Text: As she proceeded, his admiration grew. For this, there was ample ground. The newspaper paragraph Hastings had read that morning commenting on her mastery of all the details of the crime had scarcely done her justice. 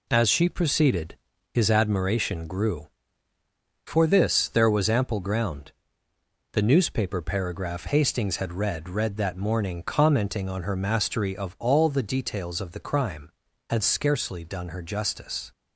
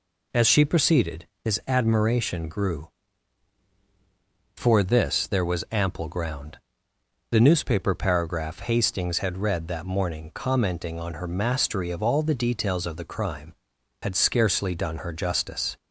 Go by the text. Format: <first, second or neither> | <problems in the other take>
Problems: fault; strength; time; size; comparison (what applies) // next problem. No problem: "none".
second | says "read" twice; at 8.8 s